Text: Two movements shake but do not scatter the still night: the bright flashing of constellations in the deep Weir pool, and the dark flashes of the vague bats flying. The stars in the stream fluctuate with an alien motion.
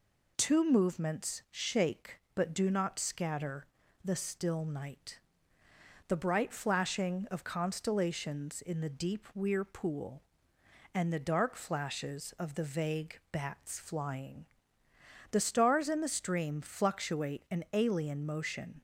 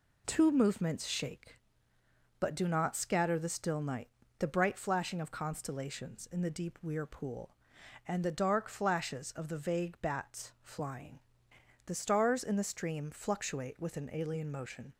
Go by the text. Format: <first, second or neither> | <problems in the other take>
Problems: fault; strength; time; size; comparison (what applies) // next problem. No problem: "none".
second | pauses between "scatter" and "the"; slight; at 3.6 s; 0.36 s long // skips "with"; at 17.4 s